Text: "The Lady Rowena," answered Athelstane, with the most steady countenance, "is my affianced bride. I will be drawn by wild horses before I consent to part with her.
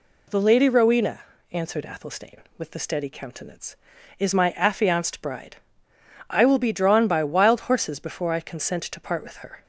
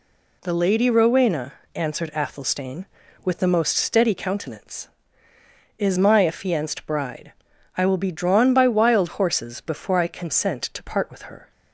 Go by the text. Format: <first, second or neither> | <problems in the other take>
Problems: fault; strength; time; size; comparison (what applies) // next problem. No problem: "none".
second | skips "most"; at 2.7 s